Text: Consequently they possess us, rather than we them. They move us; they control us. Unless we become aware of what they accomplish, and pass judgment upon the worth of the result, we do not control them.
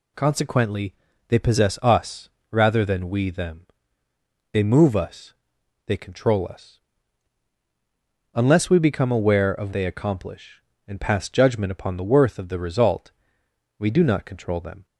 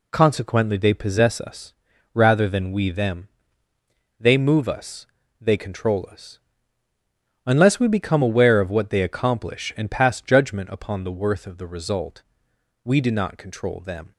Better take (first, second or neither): second